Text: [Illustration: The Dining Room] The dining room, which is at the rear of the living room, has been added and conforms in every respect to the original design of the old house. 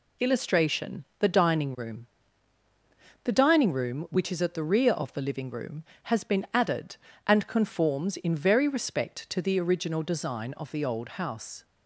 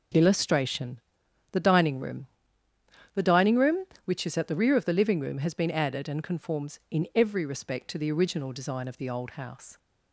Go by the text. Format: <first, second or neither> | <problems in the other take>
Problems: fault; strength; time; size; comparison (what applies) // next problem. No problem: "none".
second | pauses between "Room" and "The"; at 2.0 s; 1.1 s long; noticeable in the second // says "very" for "every"; at 8.3 s